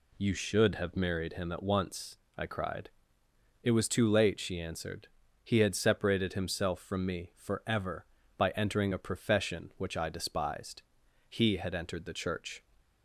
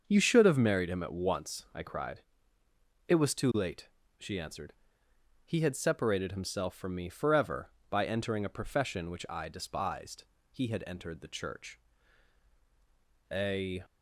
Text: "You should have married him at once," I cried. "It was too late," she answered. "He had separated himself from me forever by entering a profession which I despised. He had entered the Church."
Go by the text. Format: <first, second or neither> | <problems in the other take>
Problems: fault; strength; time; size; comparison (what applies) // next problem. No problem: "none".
first | starts louder than the rest; until 1.0 s; 6.5 dB // goes on to say "A"; from 13.3 s on; 0.50 s long